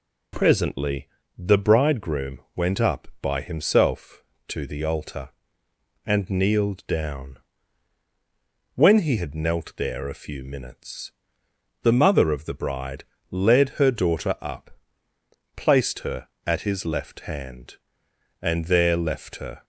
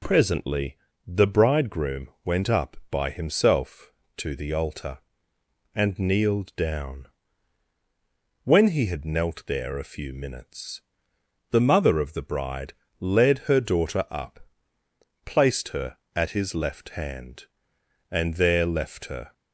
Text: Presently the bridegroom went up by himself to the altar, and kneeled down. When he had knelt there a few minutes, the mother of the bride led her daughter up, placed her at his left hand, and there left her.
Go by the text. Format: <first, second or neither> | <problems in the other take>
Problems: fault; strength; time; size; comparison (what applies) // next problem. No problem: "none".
neither | pauses between "Presently" and "the"; slight; the same in both // pauses between "bridegroom" and "went"; slight; the same in both // pauses between "bride" and "led"; slight; the same in both